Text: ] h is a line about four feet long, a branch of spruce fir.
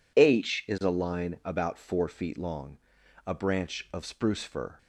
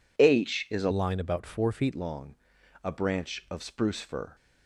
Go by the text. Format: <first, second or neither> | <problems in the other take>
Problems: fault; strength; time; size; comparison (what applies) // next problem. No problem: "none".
first | changes voice from "line" to "feet"; from 0.9 to 1.9 s; 1.0 s long